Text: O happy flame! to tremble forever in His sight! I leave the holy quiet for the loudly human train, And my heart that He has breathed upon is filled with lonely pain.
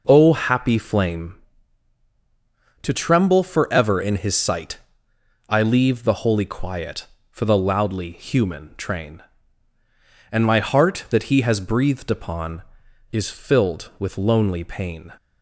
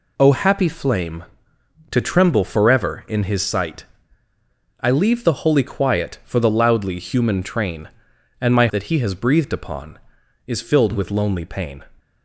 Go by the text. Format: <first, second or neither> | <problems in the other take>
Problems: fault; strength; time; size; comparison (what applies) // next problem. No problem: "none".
first | skips "heart"; at 8.6 s